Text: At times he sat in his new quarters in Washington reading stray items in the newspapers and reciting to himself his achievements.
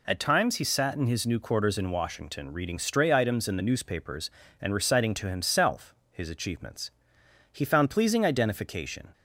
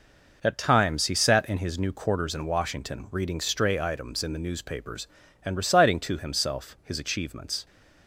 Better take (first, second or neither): second